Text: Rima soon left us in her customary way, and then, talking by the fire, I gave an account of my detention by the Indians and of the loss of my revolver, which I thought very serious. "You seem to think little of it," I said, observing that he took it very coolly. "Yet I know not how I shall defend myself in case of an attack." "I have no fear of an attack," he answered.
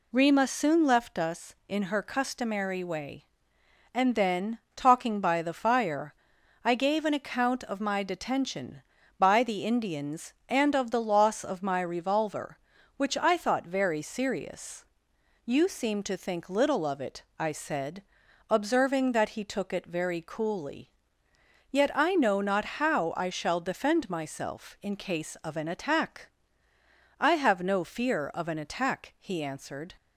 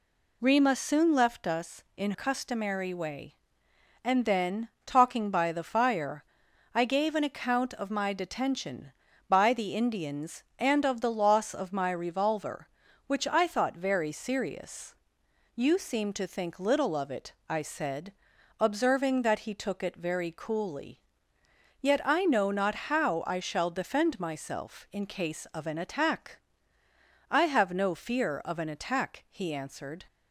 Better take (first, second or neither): first